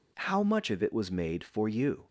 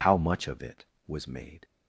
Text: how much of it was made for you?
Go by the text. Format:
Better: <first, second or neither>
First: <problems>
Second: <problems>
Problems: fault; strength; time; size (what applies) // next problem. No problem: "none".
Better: first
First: none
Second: stops before "for you"; at 1.6 s